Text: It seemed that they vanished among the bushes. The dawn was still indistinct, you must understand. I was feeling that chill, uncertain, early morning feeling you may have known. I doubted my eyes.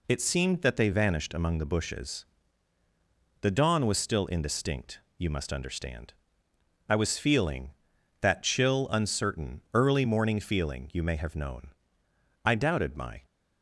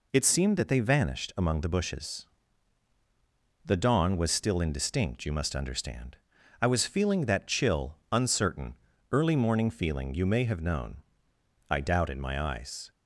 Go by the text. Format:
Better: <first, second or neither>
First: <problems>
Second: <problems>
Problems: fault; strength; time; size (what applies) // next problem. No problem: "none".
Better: second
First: stops before "eyes"; at 13.2 s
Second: none